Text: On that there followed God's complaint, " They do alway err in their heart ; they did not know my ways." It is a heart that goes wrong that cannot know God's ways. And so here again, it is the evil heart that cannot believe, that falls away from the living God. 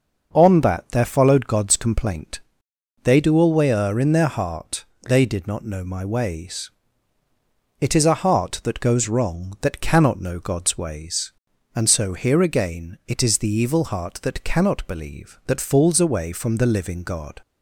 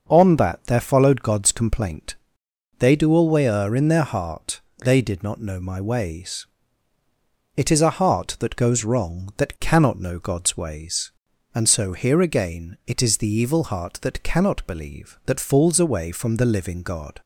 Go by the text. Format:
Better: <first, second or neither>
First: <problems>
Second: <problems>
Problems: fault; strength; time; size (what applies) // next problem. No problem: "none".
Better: neither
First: starts louder than the rest; noticeable; until 1.3 s; 6 dB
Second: starts louder than the rest; until 1.1 s; 6 dB